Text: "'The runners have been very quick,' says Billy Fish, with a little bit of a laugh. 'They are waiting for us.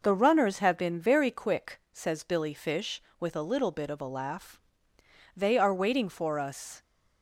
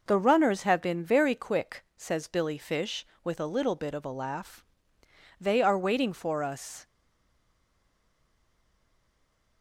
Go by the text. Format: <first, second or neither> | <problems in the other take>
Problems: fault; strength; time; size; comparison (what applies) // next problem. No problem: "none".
first | stays silent after the last word; strong; from 6.8 s on; 2.8 s long